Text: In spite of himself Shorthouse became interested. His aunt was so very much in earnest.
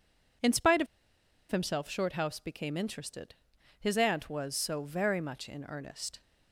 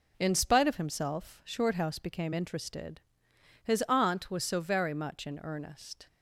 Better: second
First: pauses between "of" and "himself"; noticeable; at 0.8 s; 0.64 s long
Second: none

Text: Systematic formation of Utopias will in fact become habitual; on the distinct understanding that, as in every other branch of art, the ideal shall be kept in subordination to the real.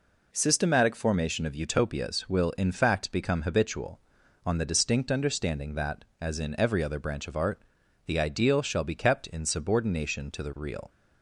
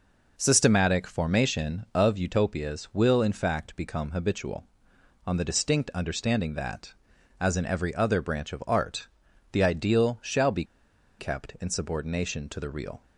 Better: first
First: none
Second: pauses between "be" and "kept"; noticeable; at 10.6 s; 0.54 s long

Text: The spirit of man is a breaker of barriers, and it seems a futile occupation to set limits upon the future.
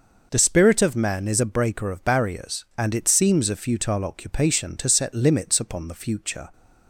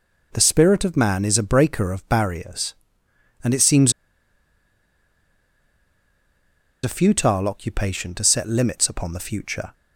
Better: first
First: none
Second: pauses between "seems" and "a"; strong; at 3.9 s; 2.9 s long

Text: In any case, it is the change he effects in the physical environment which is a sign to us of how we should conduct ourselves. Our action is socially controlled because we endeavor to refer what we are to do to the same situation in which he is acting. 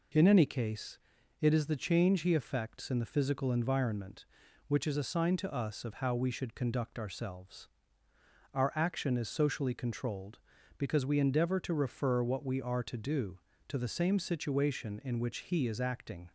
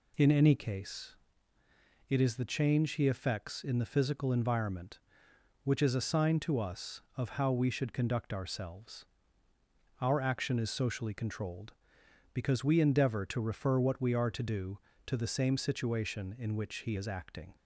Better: neither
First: none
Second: none

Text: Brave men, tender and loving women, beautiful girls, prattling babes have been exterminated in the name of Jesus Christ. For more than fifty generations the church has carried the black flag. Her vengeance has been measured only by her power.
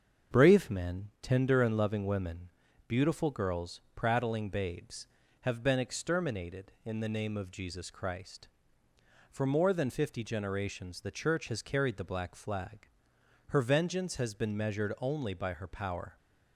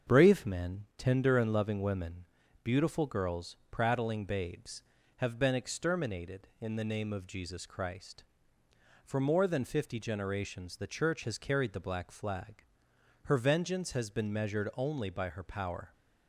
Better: neither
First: starts louder than the rest; until 1.4 s; 7 dB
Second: starts louder than the rest; until 1.1 s; 7 dB

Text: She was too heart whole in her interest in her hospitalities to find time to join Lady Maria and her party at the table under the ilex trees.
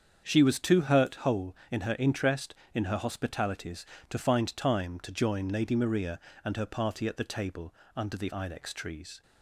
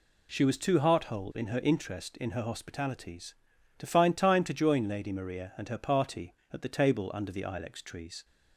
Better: second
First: starts louder than the rest; strong; until 1.2 s; 7.5 dB // says "hurt" for "heart"; at 0.8 s // pauses between "table" and "under"; slight; at 7.7 s; 0.22 s long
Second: none

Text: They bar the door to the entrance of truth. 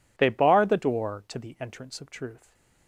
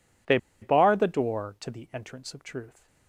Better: first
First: none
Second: pauses between "They" and "bar"; slight; at 0.3 s; 0.24 s long

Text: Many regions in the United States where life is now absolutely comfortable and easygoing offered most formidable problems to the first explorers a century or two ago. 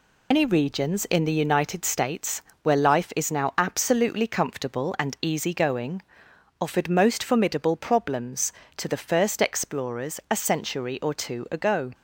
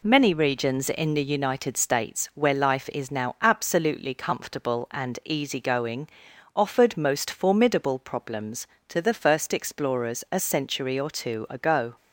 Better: second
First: loses the start of "Many"; at 0.3 s; 105 ms // pauses between "States" and "where"; slight; at 2.4 s; 0.20 s long // pauses between "easygoing" and "offered"; noticeable; at 6.0 s; 0.58 s long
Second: pauses between "easygoing" and "offered"; noticeable; at 6.0 s; 0.48 s long

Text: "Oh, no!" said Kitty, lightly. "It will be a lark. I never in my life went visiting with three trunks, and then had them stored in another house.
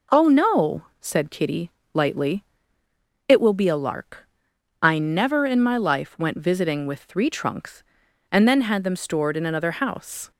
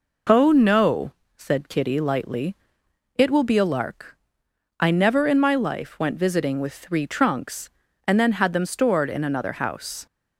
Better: neither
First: none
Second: none

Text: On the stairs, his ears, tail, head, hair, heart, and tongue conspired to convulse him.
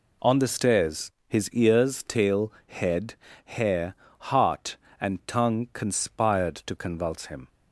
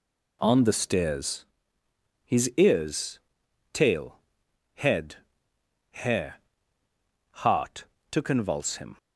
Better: first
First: none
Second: skips "and tongue conspired"; at 7.9 s

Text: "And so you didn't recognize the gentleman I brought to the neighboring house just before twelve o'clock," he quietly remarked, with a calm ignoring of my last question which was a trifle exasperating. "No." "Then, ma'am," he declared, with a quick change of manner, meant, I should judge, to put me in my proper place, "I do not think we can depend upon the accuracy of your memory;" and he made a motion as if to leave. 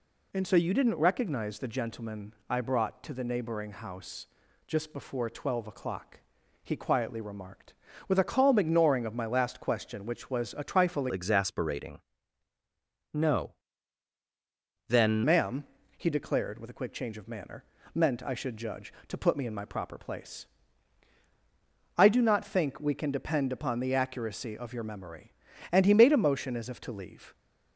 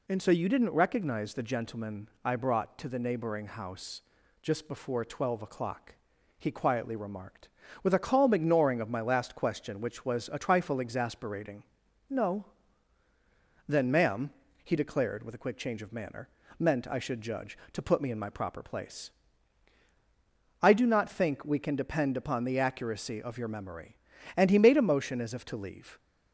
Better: second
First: pauses between "gentleman" and "I"; slight; at 2.3 s; 0.16 s long // pauses between "house" and "just"; at 4.2 s; 0.38 s long // changes voice from "exasperating" to "Then"; from 11.1 to 15.2 s; 4.1 s long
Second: pauses between "gentleman" and "I"; slight; at 2.0 s; 0.16 s long // pauses between "house" and "just"; at 4.0 s; 0.38 s long

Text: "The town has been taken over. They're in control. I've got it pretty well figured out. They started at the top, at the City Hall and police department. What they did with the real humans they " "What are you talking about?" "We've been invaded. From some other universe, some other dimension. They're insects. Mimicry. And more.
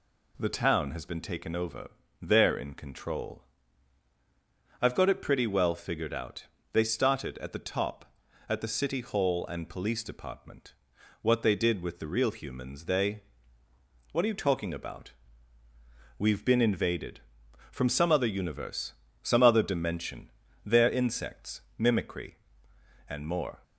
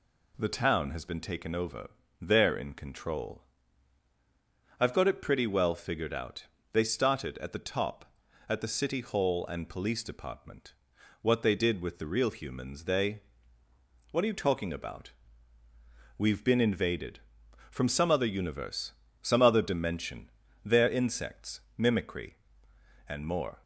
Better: neither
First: none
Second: none

